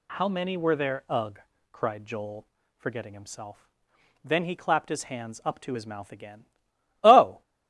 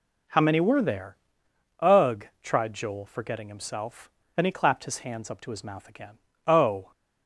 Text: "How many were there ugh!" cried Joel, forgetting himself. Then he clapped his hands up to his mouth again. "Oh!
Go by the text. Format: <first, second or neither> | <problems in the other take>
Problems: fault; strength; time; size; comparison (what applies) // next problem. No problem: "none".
first | pauses between "there" and "ugh"; noticeable; at 1.1 s; 0.62 s long // says "tried" for "cried"; at 2.4 s